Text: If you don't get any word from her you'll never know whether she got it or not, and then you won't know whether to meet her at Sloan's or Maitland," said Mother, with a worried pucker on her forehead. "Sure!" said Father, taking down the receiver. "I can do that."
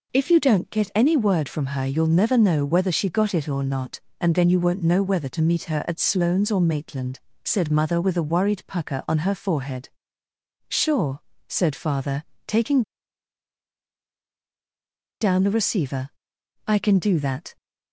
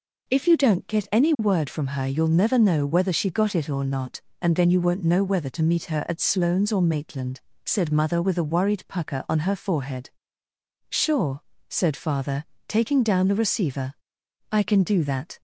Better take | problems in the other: second | pauses between "taking" and "down"; strong; at 12.8 s; 2.3 s long

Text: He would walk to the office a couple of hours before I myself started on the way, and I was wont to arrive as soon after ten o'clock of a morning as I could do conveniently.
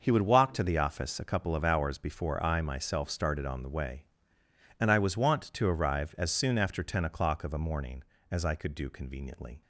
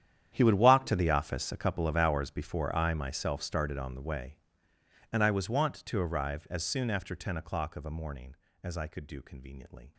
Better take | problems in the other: first | gets quieter; strong; throughout; 18 dB

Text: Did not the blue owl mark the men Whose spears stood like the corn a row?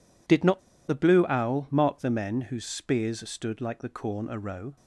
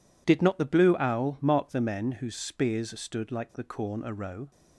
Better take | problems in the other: second | pauses between "not" and "the"; slight; at 0.5 s; 0.29 s long

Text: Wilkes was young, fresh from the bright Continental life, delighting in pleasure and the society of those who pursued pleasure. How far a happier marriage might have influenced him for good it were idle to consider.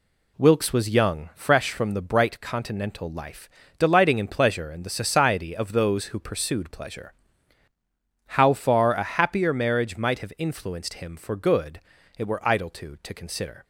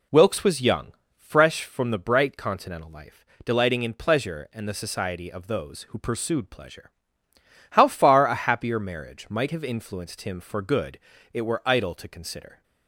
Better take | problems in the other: second | pauses between "good" and "it"; at 11.7 s; 0.38 s long; slight in the second // says "to" twice; at 13.0 s

